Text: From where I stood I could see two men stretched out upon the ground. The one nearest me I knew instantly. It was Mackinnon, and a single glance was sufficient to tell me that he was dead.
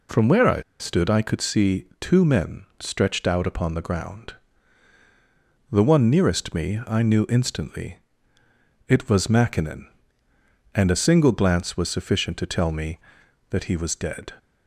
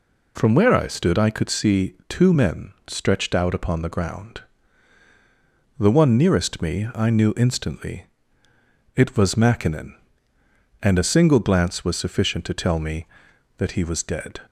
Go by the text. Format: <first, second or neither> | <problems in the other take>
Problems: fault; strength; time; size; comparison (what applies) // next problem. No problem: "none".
second | pauses between "I" and "stood"; slight; at 0.5 s; 0.19 s long // pauses between "see" and "two"; slight; at 1.8 s; 0.16 s long; slight in the second // pauses between "men" and "stretched"; slight; at 2.6 s; 0.16 s long; slight in the second